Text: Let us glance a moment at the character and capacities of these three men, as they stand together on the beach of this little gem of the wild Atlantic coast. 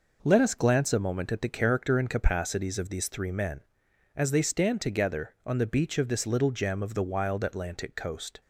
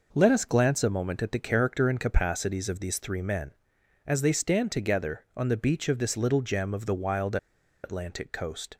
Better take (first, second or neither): first